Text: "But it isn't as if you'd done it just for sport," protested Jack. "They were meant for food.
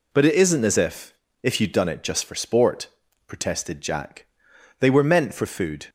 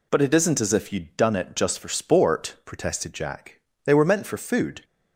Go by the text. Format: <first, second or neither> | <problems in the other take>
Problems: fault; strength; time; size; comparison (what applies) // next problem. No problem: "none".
second | says "if" twice; at 1.4 s